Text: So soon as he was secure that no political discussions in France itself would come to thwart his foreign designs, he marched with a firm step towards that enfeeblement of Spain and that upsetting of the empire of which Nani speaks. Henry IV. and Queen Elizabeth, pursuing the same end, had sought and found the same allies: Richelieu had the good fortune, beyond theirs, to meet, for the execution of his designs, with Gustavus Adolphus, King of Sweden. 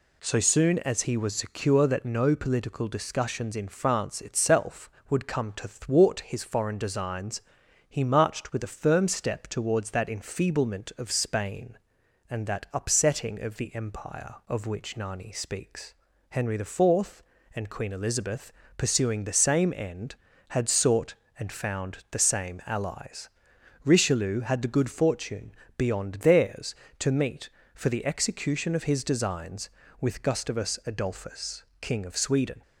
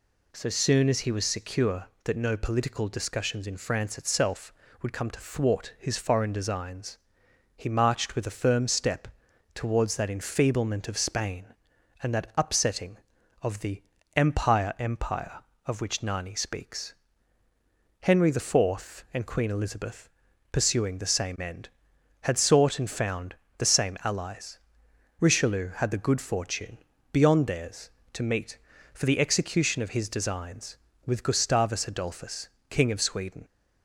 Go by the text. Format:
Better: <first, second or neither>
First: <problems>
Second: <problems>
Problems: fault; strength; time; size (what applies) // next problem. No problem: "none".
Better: first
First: none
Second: pauses between "step" and "towards"; noticeable; at 9.0 s; 0.46 s long // pauses between "the" and "empire"; slight; at 13.8 s; 0.34 s long // says "empire" twice; at 14.7 s // pauses between "found" and "the"; slight; at 23.3 s; 0.24 s long